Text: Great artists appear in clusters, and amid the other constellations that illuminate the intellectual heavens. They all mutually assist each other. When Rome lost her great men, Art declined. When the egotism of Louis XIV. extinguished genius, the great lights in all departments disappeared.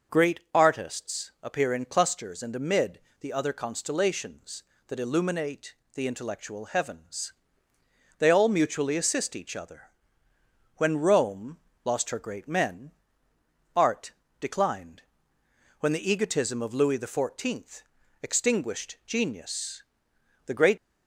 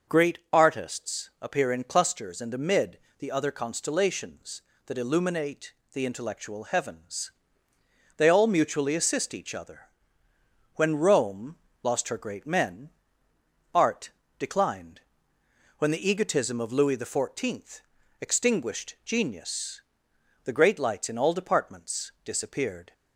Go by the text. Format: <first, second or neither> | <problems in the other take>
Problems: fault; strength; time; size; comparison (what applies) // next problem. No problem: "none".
second | pauses between "amid" and "the"; slight; at 2.9 s; 0.22 s long; slight in the second // pauses between "illuminate" and "the"; slight; at 5.7 s; 0.20 s long; slight in the second // pauses between "Rome" and "lost"; slight; at 11.5 s; 0.26 s long; slight in the second // pauses between "Art" and "declined"; slight; at 14.1 s; 0.30 s long; slight in the second // stops before "lights in all departments disappeared"; at 20.7 s